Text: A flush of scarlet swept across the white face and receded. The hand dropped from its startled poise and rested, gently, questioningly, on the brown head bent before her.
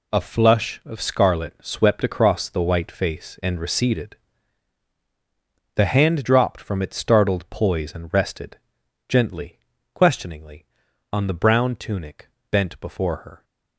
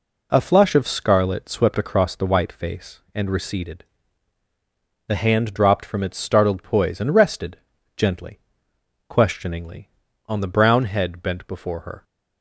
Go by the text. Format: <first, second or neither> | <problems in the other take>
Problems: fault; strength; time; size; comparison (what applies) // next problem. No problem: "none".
second | says "tunic" for "head"; at 11.7 s